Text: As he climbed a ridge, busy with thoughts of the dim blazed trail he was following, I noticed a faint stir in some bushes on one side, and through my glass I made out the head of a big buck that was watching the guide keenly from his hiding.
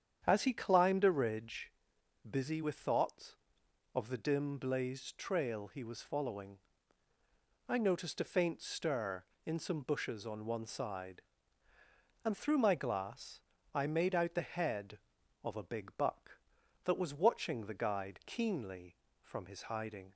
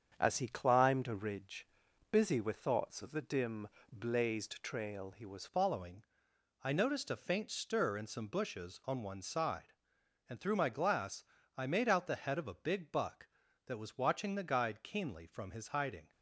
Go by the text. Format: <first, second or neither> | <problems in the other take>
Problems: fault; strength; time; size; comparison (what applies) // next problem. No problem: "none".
first | starts louder than the rest; strong; until 1.1 s; 7 dB; strong in the first // pauses between "dim" and "blazed"; slight; at 3.6 s; 0.24 s long // changes voice at "following"; from 5.4 s on; 10.7 s long // pauses between "glass" and "I"; slight; at 11.2 s; 0.32 s long; slight in the first